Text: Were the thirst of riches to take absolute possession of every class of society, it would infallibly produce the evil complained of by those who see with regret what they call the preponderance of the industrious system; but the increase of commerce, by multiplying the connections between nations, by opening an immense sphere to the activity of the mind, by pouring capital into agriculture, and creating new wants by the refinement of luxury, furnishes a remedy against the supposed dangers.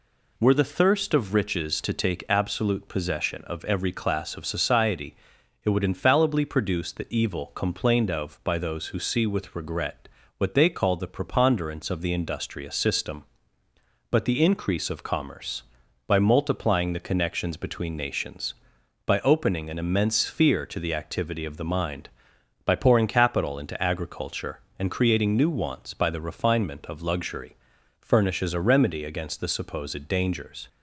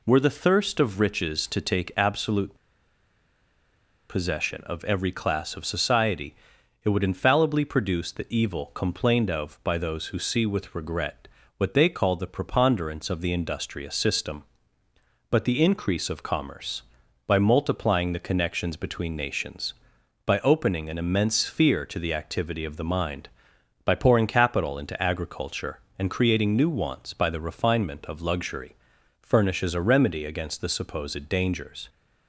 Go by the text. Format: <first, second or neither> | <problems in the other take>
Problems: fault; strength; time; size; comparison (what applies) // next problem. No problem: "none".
first | pauses between "absolute" and "possession"; strong; at 2.5 s; 1.5 s long // pauses between "regret" and "what"; slight; at 11.2 s; 0.30 s long; slight in the first